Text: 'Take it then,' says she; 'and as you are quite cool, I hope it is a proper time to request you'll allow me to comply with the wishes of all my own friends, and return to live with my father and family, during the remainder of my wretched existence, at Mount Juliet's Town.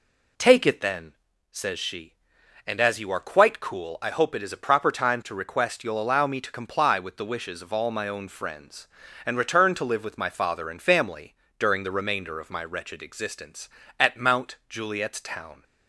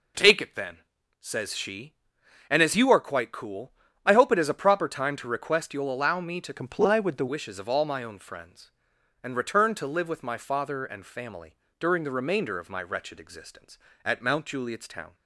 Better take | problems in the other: first | changes voice from "comply" to "the"; from 6.5 to 7.2 s; 0.7 s long

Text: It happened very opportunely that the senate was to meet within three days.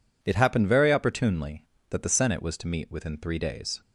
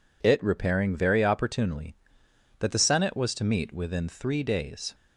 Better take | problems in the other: first | says "repairing" for "happened"; at 0.4 s

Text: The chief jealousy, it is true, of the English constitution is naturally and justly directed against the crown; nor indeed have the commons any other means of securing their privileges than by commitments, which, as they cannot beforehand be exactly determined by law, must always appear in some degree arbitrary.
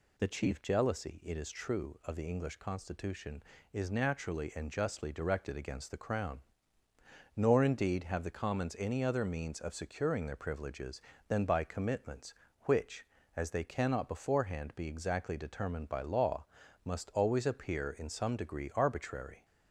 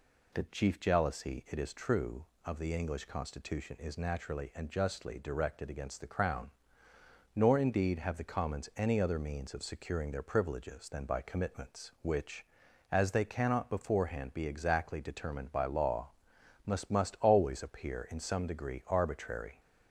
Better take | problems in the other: first | says "must" twice; at 16.8 s

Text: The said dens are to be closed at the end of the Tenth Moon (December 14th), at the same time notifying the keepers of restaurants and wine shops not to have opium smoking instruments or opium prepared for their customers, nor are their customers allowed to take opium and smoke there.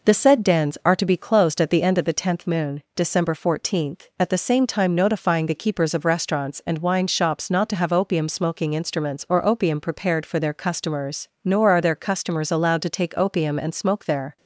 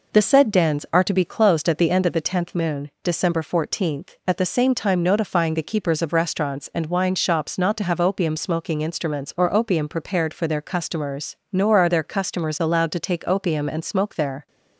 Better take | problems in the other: neither | none

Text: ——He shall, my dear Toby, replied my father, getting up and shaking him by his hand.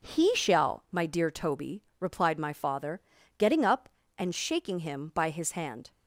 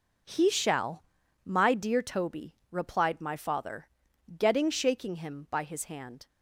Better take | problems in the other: first | skips "up and"; at 4.7 s

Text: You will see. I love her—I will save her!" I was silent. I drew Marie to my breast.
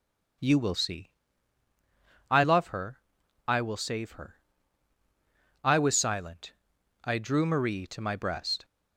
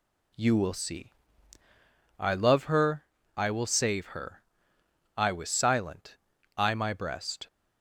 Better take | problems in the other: first | skips "drew Marie to"; at 6.7 s

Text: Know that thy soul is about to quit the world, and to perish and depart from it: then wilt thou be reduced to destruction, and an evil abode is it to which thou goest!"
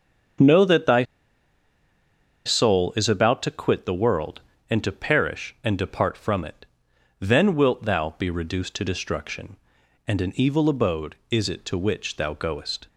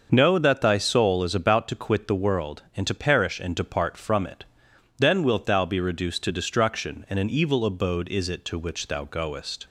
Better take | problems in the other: second | starts louder than the rest; strong; until 2.8 s; 7.5 dB; also in the second // pauses between "thy" and "soul"; strong; at 1.0 s; 1.4 s long

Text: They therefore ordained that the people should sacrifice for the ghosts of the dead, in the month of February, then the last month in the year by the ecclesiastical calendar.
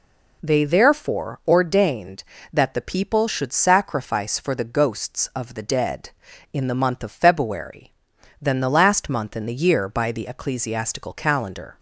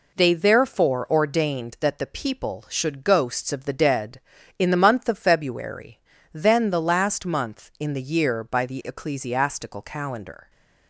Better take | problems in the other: first | skips "sacrifice for the"; at 3.0 s

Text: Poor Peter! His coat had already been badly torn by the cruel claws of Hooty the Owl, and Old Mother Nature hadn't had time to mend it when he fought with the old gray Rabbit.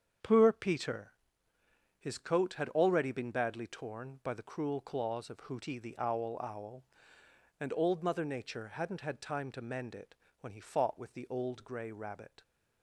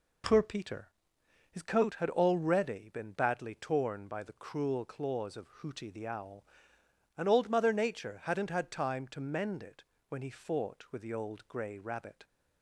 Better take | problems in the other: second | starts louder than the rest; strong; until 2.0 s; 7.5 dB // says "Owl" twice; at 6.4 s // pauses between "it" and "when"; slight; at 10.1 s; 0.26 s long; slight in the second

